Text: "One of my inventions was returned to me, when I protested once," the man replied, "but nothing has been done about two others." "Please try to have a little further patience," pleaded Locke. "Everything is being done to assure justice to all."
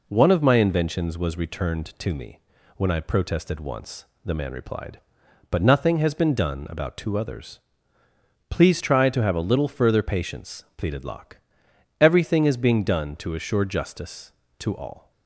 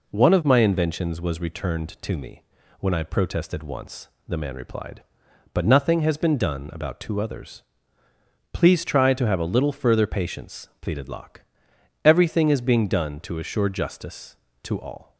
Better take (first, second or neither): neither